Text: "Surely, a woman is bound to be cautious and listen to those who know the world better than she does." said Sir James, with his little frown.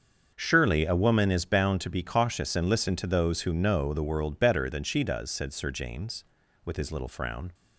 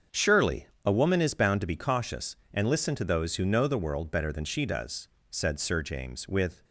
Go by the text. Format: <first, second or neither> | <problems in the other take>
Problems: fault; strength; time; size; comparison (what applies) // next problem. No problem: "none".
first | starts louder than the rest; until 1.3 s; 7 dB; also in the first // stops before "his little frown"; at 6.6 s